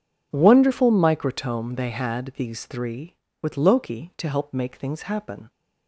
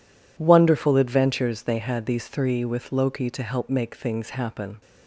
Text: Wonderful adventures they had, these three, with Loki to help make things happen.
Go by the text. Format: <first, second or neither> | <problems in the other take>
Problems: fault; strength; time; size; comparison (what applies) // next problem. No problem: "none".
second | says "microtome" for "adventures"; at 0.9 s